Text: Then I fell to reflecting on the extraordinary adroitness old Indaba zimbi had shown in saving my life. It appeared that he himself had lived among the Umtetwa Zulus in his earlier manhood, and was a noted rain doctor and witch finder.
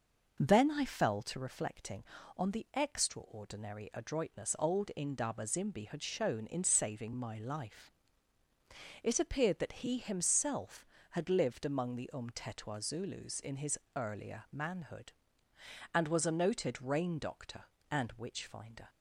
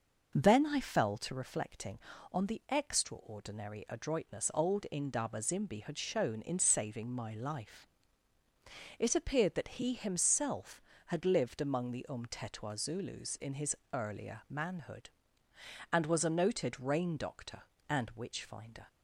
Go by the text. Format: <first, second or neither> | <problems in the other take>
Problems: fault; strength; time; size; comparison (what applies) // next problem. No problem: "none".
neither | pauses between "his" and "earlier"; slight; the same in both